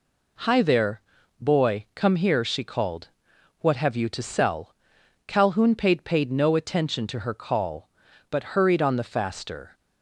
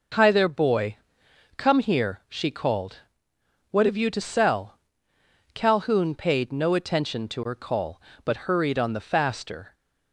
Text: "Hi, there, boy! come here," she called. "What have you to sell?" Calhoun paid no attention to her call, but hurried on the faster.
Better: second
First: says "paid" twice; at 6.0 s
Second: none

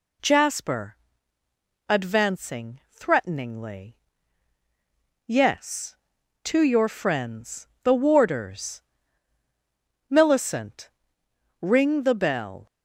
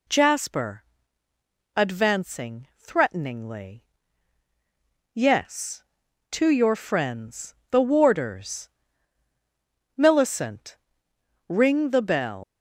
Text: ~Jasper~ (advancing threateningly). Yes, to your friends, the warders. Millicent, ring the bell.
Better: first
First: none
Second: leaves "bell" unfinished; at 12.4 s; 95 ms

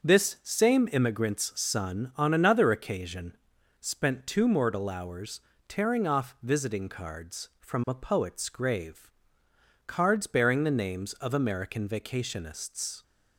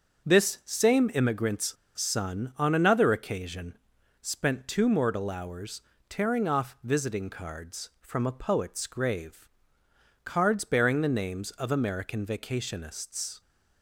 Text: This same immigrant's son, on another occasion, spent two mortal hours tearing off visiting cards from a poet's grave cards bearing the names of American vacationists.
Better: first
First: starts louder than the rest; until 1.1 s; 6.5 dB // pauses between "hours" and "tearing"; slight; at 5.3 s; 0.28 s long // pauses between "grave" and "cards"; noticeable; at 9.0 s; 0.78 s long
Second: starts louder than the rest; until 1.3 s; 6.5 dB // pauses between "immigrant's" and "son"; slight; at 1.7 s; 0.23 s long // pauses between "hours" and "tearing"; slight; at 5.8 s; 0.28 s long // pauses between "grave" and "cards"; noticeable; at 9.4 s; 0.78 s long

